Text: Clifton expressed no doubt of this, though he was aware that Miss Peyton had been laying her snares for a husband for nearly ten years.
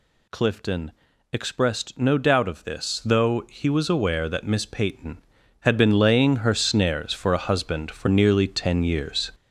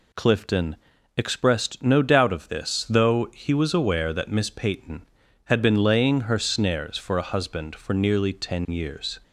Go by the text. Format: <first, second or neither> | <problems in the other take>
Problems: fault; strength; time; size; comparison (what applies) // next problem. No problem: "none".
second | gets louder; throughout; 6.5 dB // pauses between "Clifton" and "expressed"; at 0.9 s; 0.40 s long; also in the second